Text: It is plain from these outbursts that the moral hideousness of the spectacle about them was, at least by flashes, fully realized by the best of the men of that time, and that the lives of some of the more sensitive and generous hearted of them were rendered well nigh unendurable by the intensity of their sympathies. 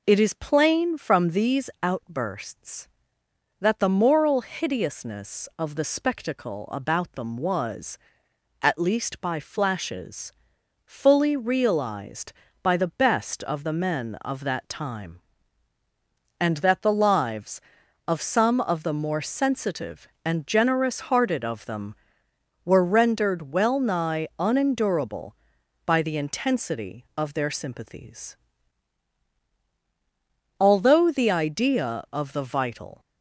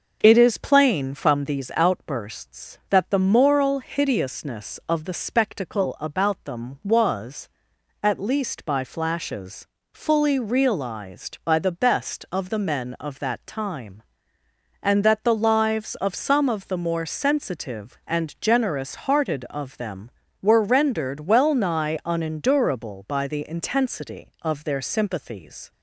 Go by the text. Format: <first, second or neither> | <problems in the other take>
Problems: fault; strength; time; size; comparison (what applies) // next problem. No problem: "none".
second | goes on to say "Although the idea of the vital"; strong; from 30.5 s on; 2.4 s long